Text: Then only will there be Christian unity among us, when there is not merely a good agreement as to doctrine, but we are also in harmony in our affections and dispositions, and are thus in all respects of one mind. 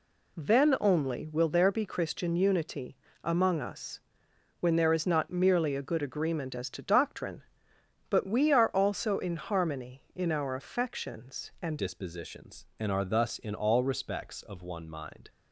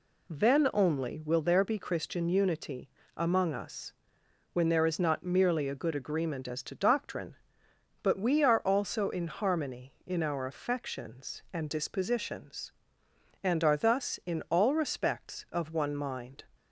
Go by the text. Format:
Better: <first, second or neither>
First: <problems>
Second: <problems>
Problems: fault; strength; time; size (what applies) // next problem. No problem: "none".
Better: second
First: pauses between "unity" and "among"; slight; at 2.9 s; 0.28 s long // changes voice at "dispositions"; from 11.7 s on; 3.5 s long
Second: pauses between "unity" and "among"; slight; at 2.8 s; 0.28 s long